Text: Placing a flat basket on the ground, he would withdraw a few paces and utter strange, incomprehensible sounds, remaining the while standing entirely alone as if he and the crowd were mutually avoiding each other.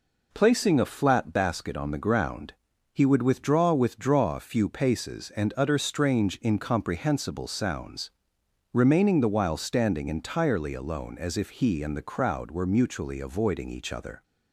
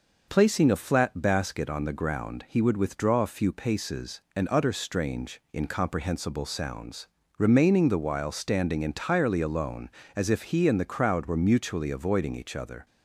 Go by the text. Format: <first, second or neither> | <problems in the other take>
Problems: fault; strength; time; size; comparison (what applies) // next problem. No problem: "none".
second | says "withdraw" twice; at 3.7 s